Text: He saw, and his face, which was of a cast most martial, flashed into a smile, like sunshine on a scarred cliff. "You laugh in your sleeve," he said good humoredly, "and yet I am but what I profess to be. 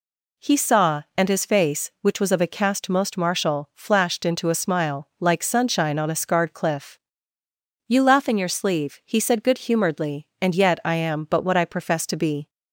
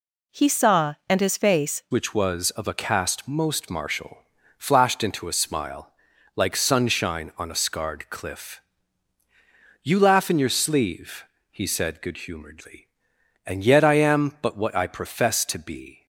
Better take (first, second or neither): first